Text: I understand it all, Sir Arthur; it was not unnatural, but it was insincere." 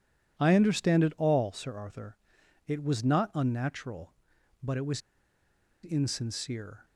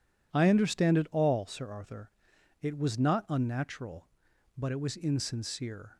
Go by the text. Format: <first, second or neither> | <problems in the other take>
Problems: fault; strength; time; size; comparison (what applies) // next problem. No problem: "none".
second | pauses between "was" and "insincere"; noticeable; at 5.0 s; 0.82 s long